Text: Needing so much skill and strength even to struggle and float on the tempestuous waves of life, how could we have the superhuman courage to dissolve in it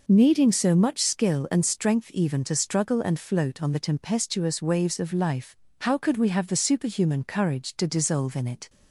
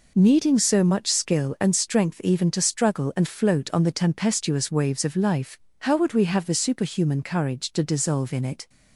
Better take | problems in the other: first | says "would" for "could"; at 5.9 s

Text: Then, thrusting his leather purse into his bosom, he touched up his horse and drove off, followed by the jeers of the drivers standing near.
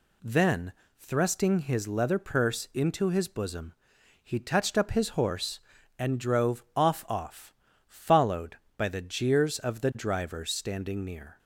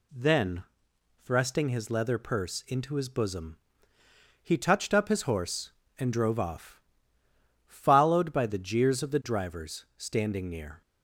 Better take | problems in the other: second | says "off" twice; at 7.0 s

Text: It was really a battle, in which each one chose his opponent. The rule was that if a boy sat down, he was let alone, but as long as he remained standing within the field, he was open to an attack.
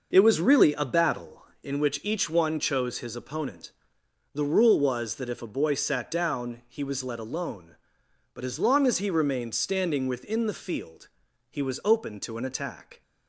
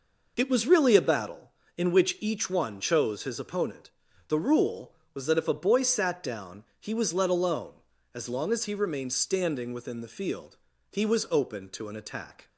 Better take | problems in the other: first | skips "but"; at 7.9 s

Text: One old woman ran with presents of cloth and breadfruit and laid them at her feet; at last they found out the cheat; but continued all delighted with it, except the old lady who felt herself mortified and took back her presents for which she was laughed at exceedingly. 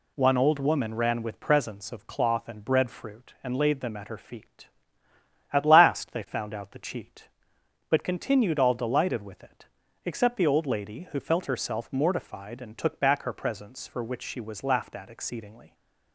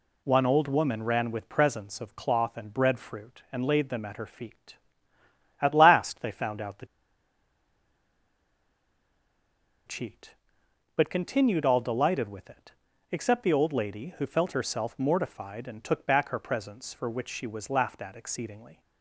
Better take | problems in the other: first | pauses between "the" and "cheat"; strong; at 6.8 s; 3.0 s long

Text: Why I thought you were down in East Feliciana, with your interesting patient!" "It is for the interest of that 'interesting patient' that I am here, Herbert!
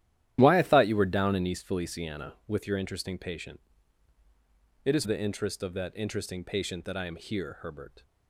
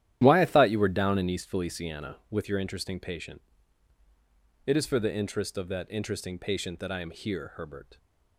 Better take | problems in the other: second | starts louder than the rest; strong; until 1.4 s; 12 dB; strong in the second // skips "for"; at 5.0 s

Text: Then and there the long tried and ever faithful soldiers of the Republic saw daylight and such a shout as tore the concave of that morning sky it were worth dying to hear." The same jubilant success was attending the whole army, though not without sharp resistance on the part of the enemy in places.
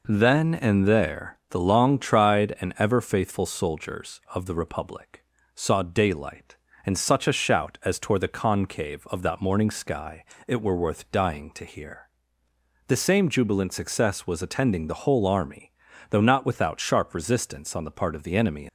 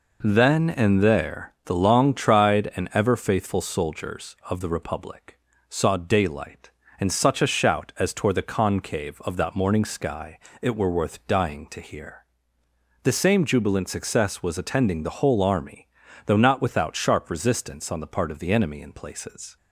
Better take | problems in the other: second | pauses between "Republic" and "saw"; slight; at 5.2 s; 0.32 s long; slight in the second // pauses between "sky" and "it"; slight; at 10.2 s; 0.22 s long; slight in the second // stops before "in places"; at 18.6 s

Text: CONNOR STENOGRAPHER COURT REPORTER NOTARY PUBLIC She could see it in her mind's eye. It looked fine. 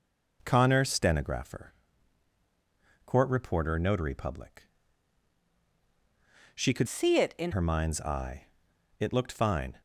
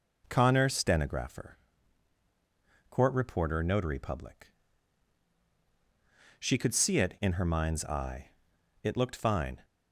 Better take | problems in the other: second | pauses between "STENOGRAPHER" and "COURT"; strong; at 1.7 s; 1.3 s long; strong in the second // pauses between "PUBLIC" and "She"; strong; at 4.6 s; 1.9 s long; strong in the second // changes voice from "see" to "in"; from 6.8 to 7.5 s; 0.7 s long

